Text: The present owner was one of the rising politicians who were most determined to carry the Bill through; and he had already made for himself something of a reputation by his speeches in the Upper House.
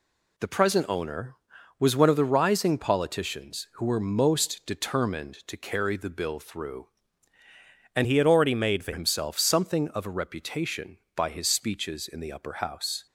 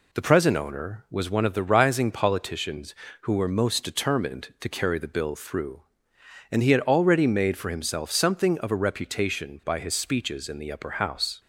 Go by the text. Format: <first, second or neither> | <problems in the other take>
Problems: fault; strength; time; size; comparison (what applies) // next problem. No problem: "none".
second | changes voice from "he" to "for"; from 8.0 to 8.9 s; 0.9 s long